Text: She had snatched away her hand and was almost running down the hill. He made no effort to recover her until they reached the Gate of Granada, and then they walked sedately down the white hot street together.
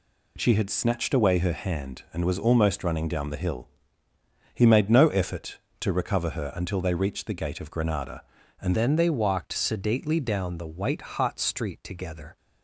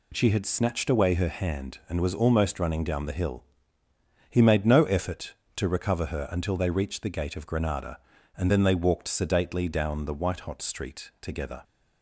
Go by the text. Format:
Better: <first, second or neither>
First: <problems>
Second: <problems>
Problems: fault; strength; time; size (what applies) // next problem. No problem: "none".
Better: second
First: changes voice at "then"; from 8.7 s on; 3.6 s long // pauses between "white" and "hot"; slight; at 11.0 s; 0.16 s long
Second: none